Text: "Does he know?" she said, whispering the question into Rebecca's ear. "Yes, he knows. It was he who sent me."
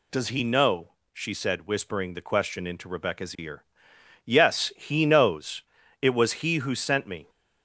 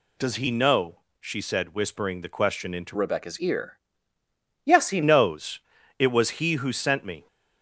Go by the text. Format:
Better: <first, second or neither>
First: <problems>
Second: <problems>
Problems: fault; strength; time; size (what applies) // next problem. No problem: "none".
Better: first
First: none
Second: changes voice from "Rebecca's" to "he"; from 2.9 to 5.0 s; 2.1 s long